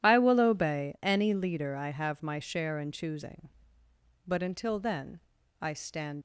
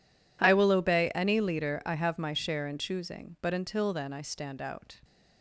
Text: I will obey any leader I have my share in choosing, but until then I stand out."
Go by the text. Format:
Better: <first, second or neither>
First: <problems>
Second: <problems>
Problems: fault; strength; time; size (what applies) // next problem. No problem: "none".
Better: second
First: pauses between "then" and "I"; at 5.2 s; 0.40 s long // stops before "out"; at 6.1 s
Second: none